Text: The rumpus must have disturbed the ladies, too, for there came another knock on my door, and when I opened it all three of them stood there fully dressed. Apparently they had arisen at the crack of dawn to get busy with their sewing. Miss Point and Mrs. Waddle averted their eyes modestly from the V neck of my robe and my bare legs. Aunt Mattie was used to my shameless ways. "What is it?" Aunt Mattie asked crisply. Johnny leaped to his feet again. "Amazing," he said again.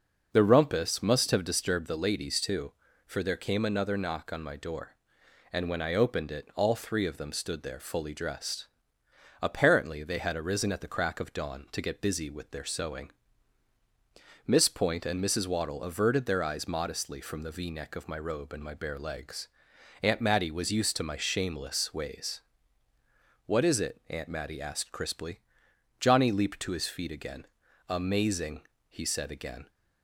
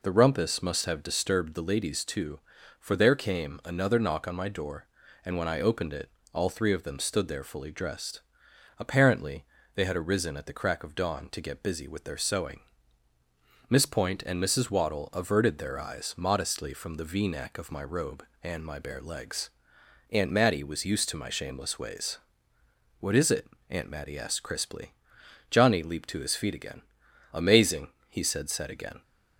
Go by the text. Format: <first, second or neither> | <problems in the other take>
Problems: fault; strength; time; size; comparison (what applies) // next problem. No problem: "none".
first | pauses between "it" and "all"; slight; at 6.0 s; 0.24 s long // pauses between "Apparently" and "they"; slight; at 9.4 s; 0.32 s long // says "said" twice; at 28.4 s